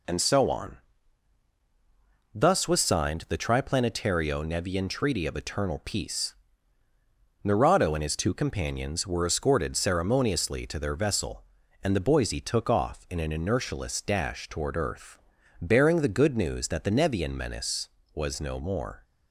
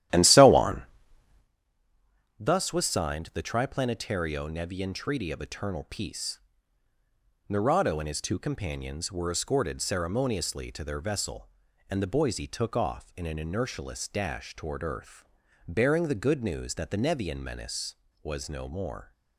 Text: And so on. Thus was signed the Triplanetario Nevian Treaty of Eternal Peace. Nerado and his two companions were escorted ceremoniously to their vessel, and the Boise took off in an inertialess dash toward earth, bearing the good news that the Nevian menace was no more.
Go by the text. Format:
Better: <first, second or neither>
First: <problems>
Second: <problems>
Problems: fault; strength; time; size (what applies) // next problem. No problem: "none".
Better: first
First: none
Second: starts louder than the rest; strong; until 1.5 s; 12.5 dB